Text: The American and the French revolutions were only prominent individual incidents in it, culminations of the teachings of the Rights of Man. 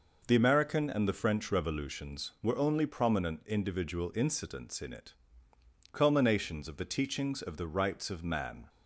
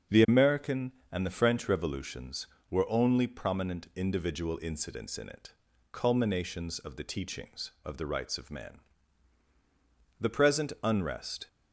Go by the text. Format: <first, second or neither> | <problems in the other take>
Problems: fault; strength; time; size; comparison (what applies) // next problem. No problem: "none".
first | starts louder than the rest; until 1.3 s; 6.5 dB // goes on to say "The present unrest"; noticeable; from 10.1 s on; 1.2 s long